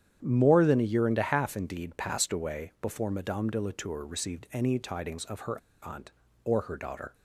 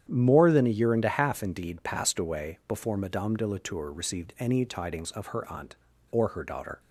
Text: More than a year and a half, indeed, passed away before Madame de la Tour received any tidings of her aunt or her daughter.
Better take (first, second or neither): second